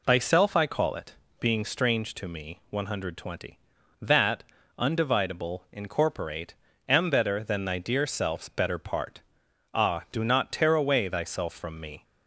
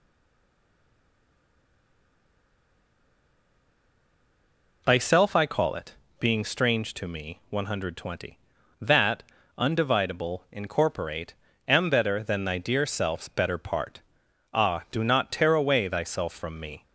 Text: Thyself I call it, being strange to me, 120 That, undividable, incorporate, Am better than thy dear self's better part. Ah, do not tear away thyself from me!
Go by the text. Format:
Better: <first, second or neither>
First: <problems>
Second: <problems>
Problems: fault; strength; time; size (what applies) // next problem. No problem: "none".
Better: first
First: none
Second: stays silent before the first word; strong; until 4.8 s; 4.8 s long